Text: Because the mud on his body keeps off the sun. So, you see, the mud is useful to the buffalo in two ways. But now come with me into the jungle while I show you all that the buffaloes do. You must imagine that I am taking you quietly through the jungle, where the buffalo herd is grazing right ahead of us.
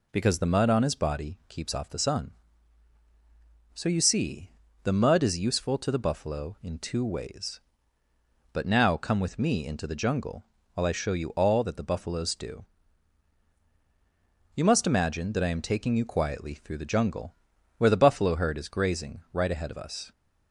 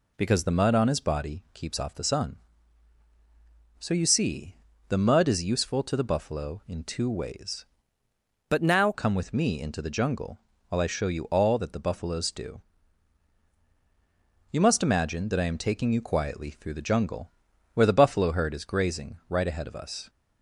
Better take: first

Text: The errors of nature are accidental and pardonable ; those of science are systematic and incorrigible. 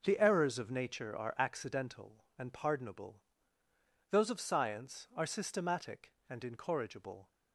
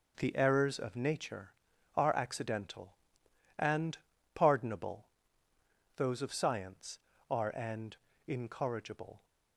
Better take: first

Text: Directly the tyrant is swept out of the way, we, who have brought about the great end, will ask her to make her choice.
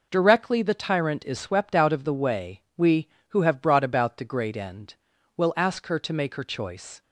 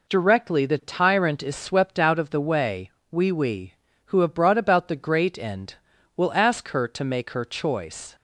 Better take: first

